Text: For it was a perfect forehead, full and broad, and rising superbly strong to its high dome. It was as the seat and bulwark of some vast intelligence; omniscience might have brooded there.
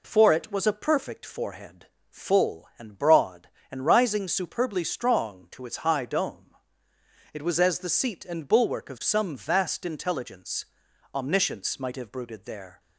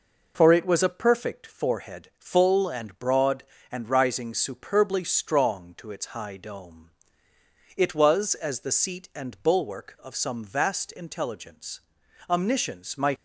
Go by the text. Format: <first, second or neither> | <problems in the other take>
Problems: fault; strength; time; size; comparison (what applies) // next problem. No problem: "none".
first | stops before "have brooded there"; at 13.1 s